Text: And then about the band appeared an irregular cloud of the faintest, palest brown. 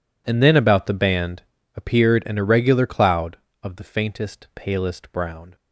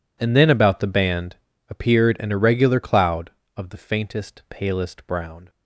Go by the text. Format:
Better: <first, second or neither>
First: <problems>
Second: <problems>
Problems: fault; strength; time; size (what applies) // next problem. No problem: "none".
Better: neither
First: pauses between "band" and "appeared"; slight; at 1.4 s; 0.32 s long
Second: pauses between "band" and "appeared"; slight; at 1.3 s; 0.32 s long